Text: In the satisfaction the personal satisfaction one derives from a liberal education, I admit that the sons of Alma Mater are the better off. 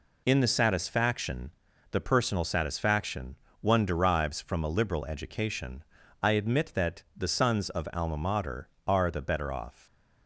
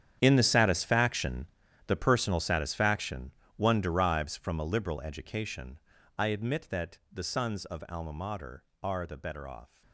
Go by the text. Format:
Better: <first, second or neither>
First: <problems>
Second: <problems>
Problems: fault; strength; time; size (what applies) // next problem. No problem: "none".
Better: first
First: pauses between "satisfaction" and "the"; at 1.4 s; 0.42 s long // pauses between "satisfaction" and "one"; slight; at 3.3 s; 0.26 s long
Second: gets quieter; strong; throughout; 17 dB // pauses between "satisfaction" and "the"; at 1.4 s; 0.42 s long // pauses between "satisfaction" and "one"; slight; at 3.3 s; 0.26 s long